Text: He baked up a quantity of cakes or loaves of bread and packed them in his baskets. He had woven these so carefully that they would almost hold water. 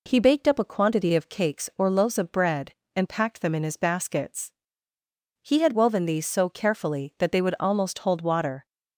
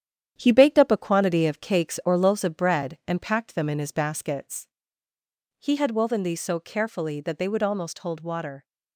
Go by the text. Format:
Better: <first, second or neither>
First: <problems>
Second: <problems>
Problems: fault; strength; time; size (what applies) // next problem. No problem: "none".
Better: first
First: none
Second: gets quieter; noticeable; throughout; 5.5 dB